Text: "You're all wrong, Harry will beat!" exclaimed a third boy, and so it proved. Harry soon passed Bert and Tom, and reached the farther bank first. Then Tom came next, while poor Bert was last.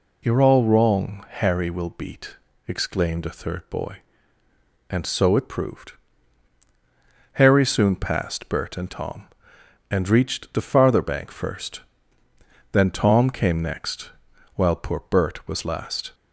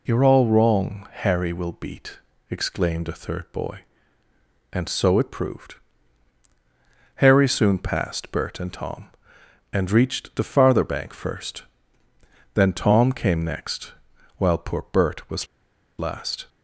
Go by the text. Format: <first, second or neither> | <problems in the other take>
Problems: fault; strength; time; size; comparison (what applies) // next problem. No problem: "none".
first | pauses between "was" and "last"; noticeable; at 15.4 s; 0.53 s long